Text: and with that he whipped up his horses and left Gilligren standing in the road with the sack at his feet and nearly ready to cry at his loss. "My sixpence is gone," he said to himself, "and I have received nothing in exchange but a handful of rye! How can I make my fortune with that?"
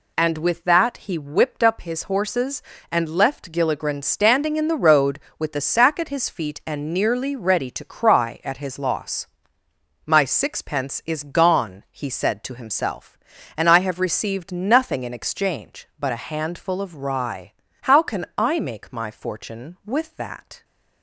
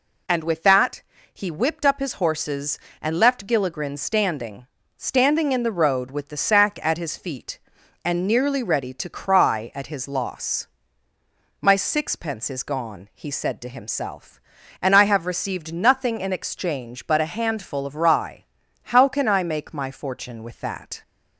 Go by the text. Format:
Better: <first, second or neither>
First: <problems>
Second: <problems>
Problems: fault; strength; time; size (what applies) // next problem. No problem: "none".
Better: first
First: none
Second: pauses between "that" and "he"; slight; at 1.0 s; 0.30 s long // says "standing" twice; at 4.9 s